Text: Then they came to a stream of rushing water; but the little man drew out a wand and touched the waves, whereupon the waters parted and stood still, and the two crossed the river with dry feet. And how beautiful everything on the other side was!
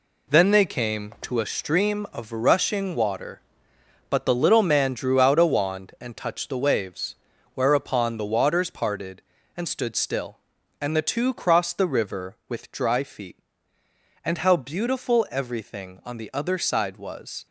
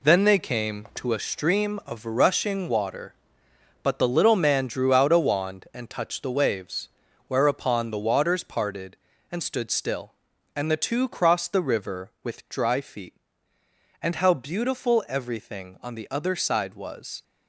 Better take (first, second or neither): neither